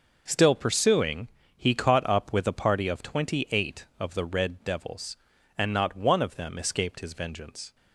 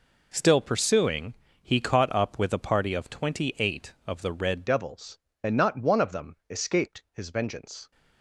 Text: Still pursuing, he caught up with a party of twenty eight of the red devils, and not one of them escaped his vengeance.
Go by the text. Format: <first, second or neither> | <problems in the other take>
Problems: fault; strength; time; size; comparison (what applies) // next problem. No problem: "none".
first | changes voice at "devils"; from 4.6 s on; 3.3 s long